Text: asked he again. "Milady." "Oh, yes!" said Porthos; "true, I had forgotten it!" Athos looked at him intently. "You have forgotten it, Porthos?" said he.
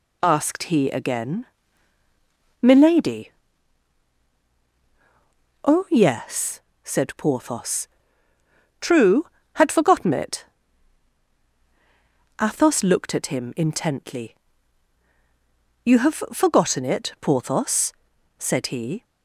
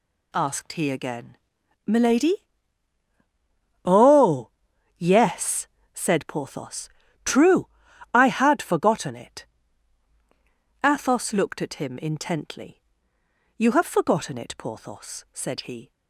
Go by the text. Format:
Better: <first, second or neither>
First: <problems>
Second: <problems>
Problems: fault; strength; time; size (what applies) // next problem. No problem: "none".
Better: second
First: skips "I"; at 9.4 s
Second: none